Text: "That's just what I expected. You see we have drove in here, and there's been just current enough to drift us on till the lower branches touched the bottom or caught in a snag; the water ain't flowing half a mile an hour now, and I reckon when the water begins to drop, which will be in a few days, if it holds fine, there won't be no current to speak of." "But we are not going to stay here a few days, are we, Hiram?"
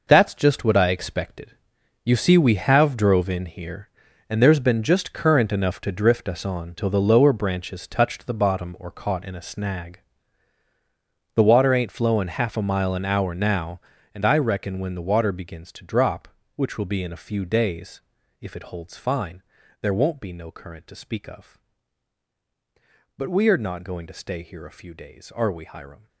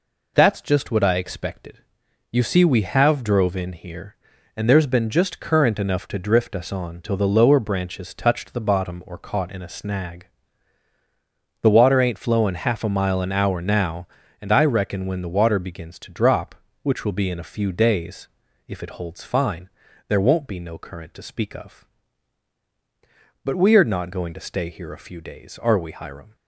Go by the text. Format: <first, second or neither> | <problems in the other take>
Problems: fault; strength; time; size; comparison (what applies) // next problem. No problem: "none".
second | gets quieter; strong; throughout; 11 dB